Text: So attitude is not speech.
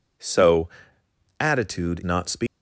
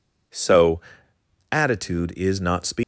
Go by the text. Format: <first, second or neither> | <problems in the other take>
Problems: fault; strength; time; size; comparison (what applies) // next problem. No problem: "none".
second | pauses between "So" and "attitude"; noticeable; at 0.6 s; 0.70 s long; noticeable in the second // skips "is"; at 2.0 s